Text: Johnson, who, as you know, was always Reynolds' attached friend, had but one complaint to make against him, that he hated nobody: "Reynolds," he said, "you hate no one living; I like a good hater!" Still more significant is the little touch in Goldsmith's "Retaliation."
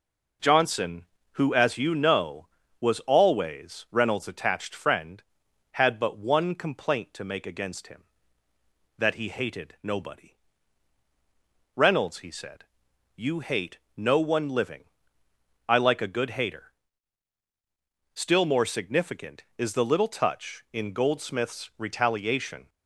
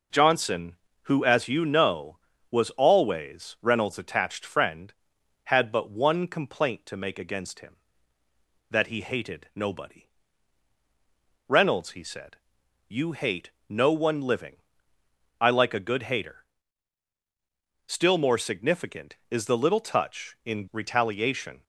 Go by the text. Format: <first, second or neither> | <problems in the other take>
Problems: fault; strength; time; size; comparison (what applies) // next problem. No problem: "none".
first | pauses between "hate" and "no"; slight; at 13.5 s; 0.18 s long; slight in the first // skips "Goldsmith's"; at 20.6 s